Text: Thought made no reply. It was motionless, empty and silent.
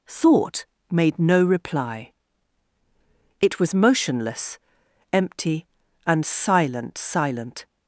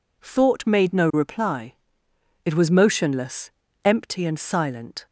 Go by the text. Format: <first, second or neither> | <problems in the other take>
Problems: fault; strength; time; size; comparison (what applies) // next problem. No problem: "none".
second | pauses between "Thought" and "made"; slight; at 0.6 s; 0.24 s long // says "silent" twice; at 6.9 s